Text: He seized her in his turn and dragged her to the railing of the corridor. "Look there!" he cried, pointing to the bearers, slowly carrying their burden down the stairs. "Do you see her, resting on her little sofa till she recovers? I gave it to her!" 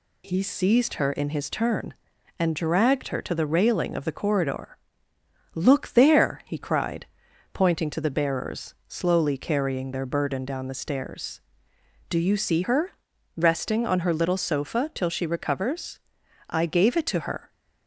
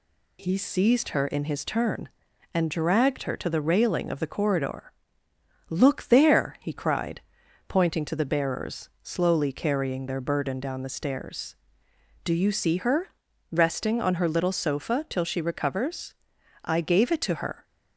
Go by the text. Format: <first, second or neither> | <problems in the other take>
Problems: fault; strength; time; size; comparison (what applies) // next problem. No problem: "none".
neither | none